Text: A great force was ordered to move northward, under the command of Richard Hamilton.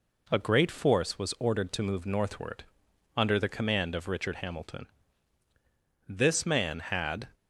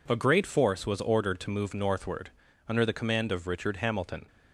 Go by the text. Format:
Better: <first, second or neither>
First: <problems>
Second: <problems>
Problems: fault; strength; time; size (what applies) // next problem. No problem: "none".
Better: second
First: goes on to say "This man had"; noticeable; from 6.0 s on; 1.2 s long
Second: none